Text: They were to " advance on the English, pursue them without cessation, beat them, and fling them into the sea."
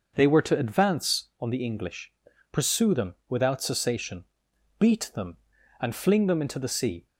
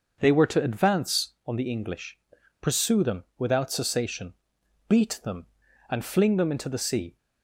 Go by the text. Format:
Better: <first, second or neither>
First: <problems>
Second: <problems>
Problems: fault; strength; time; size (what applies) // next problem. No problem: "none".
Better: neither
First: none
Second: none